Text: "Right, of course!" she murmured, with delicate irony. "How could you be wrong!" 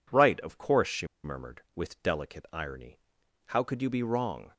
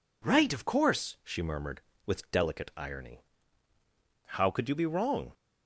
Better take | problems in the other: second | pauses between "she" and "murmured"; slight; at 1.0 s; 0.17 s long

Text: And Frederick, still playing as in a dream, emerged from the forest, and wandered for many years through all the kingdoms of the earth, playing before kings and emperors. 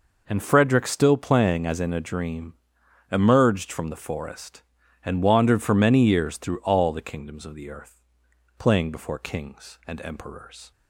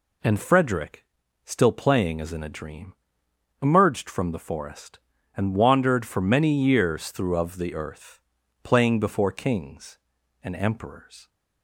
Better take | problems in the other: first | skips "all the kingdoms"; at 7.3 s

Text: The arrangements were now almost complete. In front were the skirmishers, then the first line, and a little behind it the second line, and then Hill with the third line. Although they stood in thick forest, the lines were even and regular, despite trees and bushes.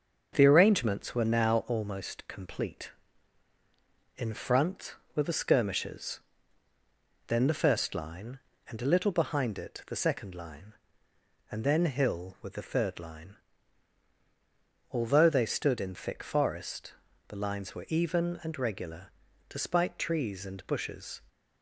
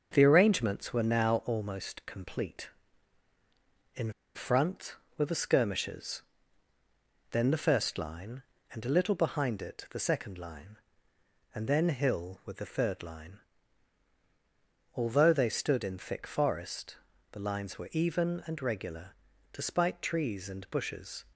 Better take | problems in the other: first | starts louder than the rest; until 1.1 s; 6.5 dB; also in the first // pauses between "In" and "front"; slight; at 4.1 s; 0.22 s long

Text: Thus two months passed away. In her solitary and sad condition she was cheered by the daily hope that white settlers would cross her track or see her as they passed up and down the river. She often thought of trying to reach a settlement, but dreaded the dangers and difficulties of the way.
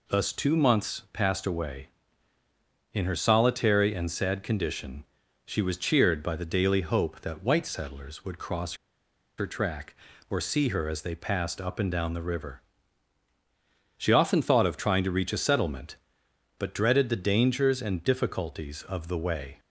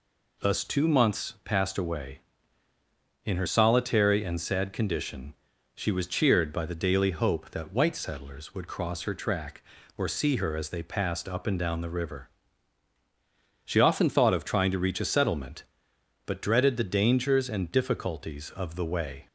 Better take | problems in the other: second | pauses between "condition" and "she"; at 5.0 s; 0.42 s long; also in the second // pauses between "cross" and "her"; noticeable; at 8.7 s; 0.63 s long

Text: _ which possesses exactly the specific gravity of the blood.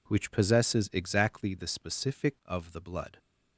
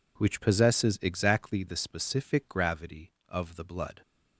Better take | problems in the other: second | skips "gravity"; at 2.4 s

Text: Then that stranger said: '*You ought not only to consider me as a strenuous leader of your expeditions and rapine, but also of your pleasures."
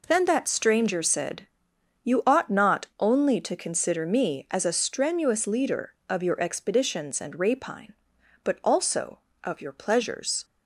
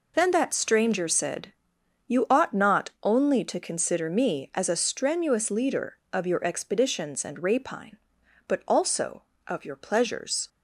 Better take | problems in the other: first | loses the start of "Then"; at 0.1 s; 35 ms

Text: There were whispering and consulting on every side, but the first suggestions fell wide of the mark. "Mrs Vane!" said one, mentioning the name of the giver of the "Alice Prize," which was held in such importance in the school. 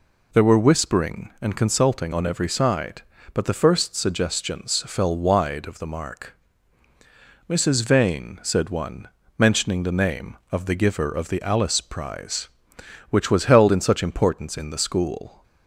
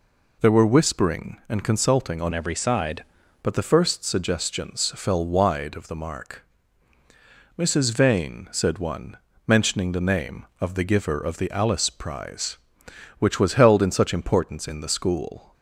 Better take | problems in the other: first | changes voice from "every" to "side"; from 2.3 to 3.0 s; 0.7 s long

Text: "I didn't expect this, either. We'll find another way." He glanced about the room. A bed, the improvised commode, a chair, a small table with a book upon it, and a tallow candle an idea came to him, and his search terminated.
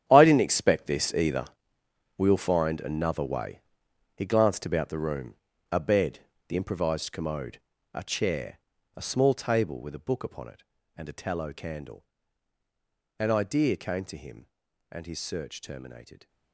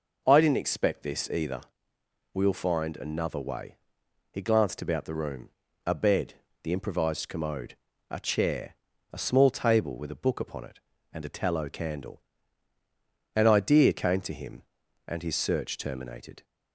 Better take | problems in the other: second | gets quieter; strong; throughout; 14.5 dB // pauses between "candle" and "an"; at 12.0 s; 1.1 s long; also in the second

